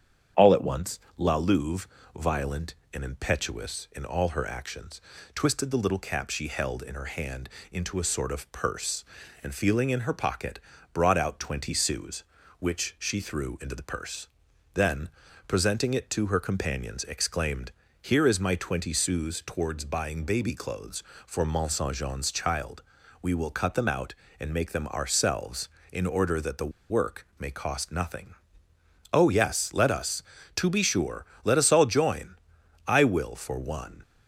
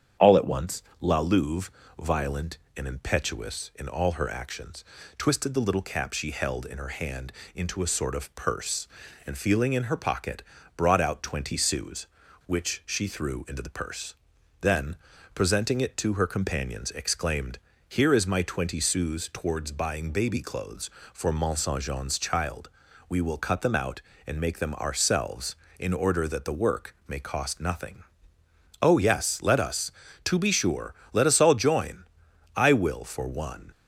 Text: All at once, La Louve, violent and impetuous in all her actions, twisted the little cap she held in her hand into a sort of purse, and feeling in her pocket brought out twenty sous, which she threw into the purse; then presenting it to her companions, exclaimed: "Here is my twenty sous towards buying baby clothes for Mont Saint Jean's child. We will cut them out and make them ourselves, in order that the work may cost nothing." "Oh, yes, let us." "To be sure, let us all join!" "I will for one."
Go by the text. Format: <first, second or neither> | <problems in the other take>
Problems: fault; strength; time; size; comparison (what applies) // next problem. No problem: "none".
second | starts louder than the rest; strong; until 1.5 s; 8.5 dB; strong in the second // pauses between "hand" and "into"; slight; at 7.4 s; 0.24 s long; slight in the second // pauses between "pocket" and "brought"; slight; at 10.5 s; 0.32 s long; slight in the second // pauses between "then" and "presenting"; at 15.0 s; 0.40 s long; also in the second // pauses between "the" and "work"; slight; at 26.7 s; 0.20 s long